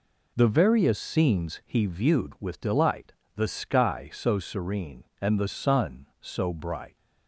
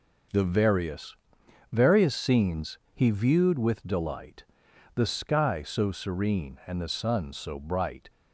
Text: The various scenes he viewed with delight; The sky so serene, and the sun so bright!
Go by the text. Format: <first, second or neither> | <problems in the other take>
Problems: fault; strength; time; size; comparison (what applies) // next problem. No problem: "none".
first | says "various" twice; at 1.7 s // pauses between "scenes" and "he"; slight; at 2.7 s; 0.16 s long